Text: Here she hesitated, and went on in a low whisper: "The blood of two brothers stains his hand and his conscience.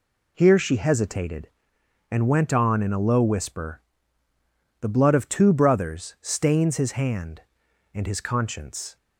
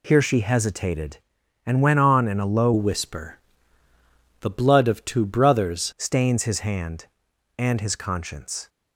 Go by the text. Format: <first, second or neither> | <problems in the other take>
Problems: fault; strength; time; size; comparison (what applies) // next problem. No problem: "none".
first | changes voice from "whisper" to "brothers"; from 2.7 to 5.9 s; 3.2 s long